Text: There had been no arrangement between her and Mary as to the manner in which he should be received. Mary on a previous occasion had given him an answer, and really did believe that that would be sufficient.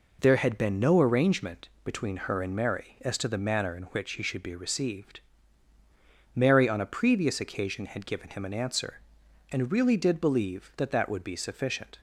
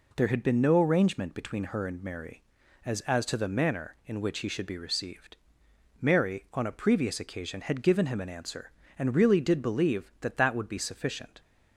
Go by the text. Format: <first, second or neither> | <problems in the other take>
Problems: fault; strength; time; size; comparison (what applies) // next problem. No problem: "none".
first | says "as" twice; at 3.0 s